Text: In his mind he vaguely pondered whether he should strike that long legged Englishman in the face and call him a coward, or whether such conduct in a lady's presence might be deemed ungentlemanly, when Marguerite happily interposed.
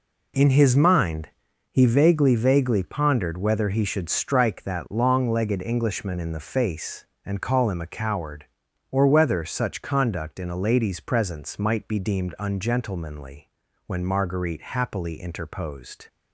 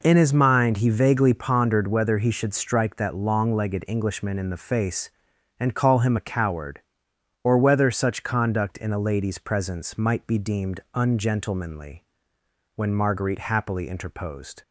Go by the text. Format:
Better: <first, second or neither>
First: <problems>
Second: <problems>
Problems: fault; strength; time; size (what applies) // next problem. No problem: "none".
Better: second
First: pauses between "mind" and "he"; at 1.2 s; 0.42 s long // says "vaguely" twice; at 2.3 s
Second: none